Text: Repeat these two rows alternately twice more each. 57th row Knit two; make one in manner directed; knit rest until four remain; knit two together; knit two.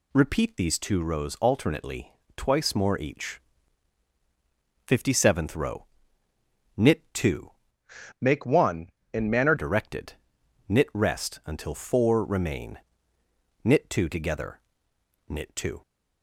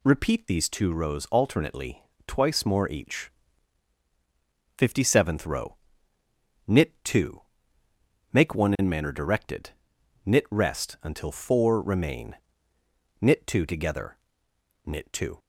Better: second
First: pauses between "alternately" and "twice"; slight; at 2.1 s; 0.24 s long // pauses between "row" and "Knit"; noticeable; at 5.8 s; 0.90 s long // changes voice from "make" to "manner"; from 8.1 to 9.5 s; 1.4 s long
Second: pauses between "alternately" and "twice"; slight; at 2.0 s; 0.24 s long // pauses between "row" and "Knit"; noticeable; at 5.7 s; 0.90 s long

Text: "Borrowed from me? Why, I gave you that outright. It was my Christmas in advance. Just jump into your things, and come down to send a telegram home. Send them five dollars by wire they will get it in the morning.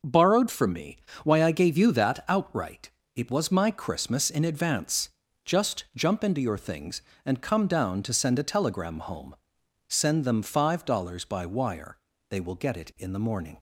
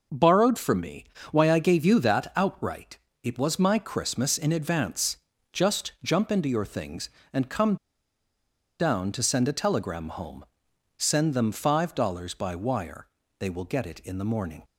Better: first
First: pauses between "wire" and "they"; slight; at 11.9 s; 0.32 s long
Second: pauses between "come" and "down"; at 7.7 s; 1.0 s long // pauses between "wire" and "they"; slight; at 13.0 s; 0.32 s long

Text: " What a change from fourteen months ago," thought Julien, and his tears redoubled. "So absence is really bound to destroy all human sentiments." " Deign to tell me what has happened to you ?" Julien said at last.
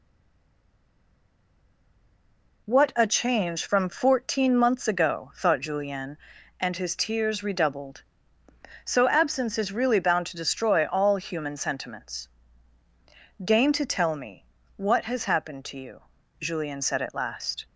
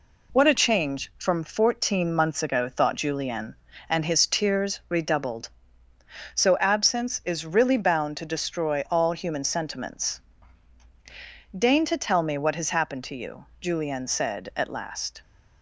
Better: second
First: stays silent before the first word; strong; until 2.6 s; 2.6 s long // pauses between "me" and "what"; slight; at 14.4 s; 0.32 s long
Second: none

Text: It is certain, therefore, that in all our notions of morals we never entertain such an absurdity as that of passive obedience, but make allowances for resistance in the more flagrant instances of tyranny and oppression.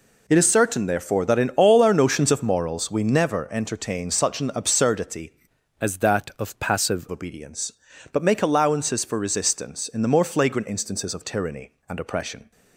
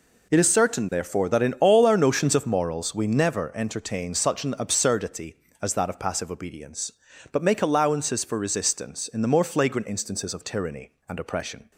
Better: second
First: changes voice from "as" to "passive"; from 5.7 to 7.0 s; 1.3 s long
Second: none

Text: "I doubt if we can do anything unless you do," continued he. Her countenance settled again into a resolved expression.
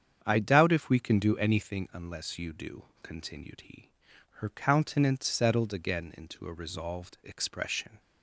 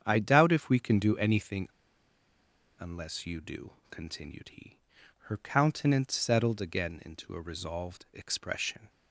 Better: first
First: starts louder than the rest; strong; until 1.2 s; 8 dB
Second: starts louder than the rest; strong; until 1.0 s; 8 dB // pauses between "anything" and "unless"; at 1.6 s; 1.1 s long

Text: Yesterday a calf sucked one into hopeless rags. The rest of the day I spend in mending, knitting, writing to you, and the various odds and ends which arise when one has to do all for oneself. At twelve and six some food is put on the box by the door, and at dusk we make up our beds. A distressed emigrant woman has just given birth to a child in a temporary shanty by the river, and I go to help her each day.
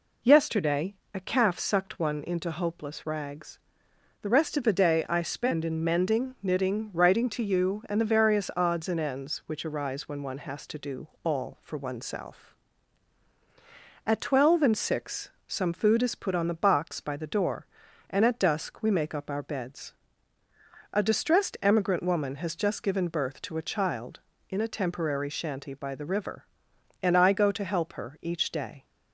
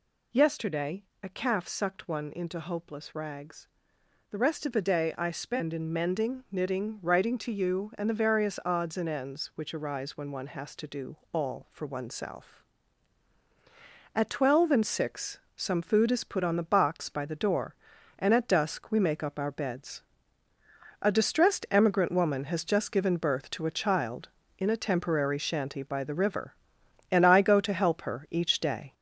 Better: first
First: pauses between "Yesterday" and "a"; slight; at 0.9 s; 0.18 s long // pauses between "do" and "all"; slight; at 11.0 s; 0.16 s long // pauses between "six" and "some"; slight; at 15.3 s; 0.18 s long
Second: gets louder; noticeable; throughout; 4 dB // pauses between "Yesterday" and "a"; slight; at 1.0 s; 0.18 s long // pauses between "do" and "all"; slight; at 11.1 s; 0.16 s long // pauses between "six" and "some"; slight; at 15.3 s; 0.18 s long

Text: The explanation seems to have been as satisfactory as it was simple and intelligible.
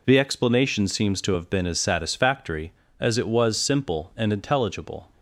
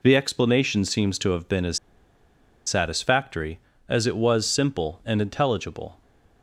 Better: first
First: none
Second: pauses between "as" and "satisfactory"; noticeable; at 1.7 s; 0.88 s long

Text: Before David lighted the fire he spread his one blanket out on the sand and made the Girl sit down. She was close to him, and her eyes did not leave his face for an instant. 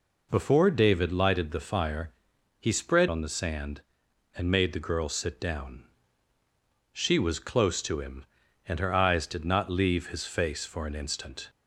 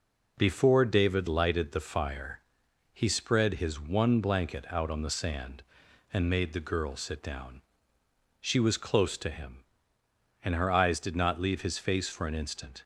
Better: second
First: pauses between "fire" and "he"; noticeable; at 2.1 s; 0.48 s long // skips "his one blanket out"; at 3.0 s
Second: pauses between "fire" and "he"; noticeable; at 2.4 s; 0.52 s long

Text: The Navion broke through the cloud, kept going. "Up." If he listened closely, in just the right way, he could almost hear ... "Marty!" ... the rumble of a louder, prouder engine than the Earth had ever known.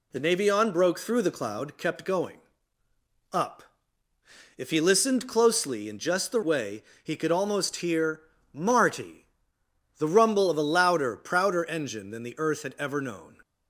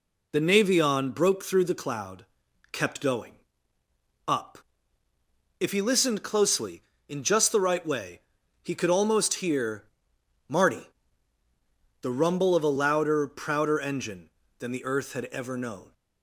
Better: second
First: skips "right"; at 6.4 s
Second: none

